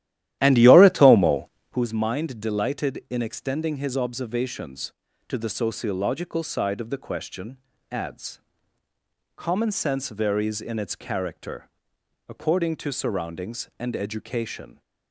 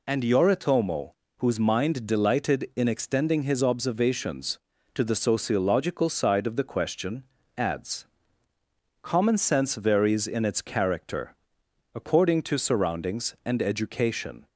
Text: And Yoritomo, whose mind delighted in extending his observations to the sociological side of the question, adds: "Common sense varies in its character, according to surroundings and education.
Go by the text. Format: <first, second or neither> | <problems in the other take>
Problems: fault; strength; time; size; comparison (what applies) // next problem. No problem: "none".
second | starts louder than the rest; strong; until 1.8 s; 13 dB